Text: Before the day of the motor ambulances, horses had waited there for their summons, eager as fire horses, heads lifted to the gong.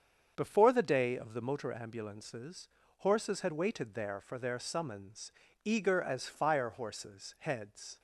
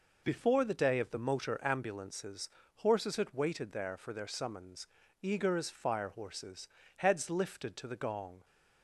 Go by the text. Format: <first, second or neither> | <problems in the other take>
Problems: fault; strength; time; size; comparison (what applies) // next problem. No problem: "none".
second | starts louder than the rest; strong; until 1.3 s; 7.5 dB // stops before "lifted to the gong"; at 7.9 s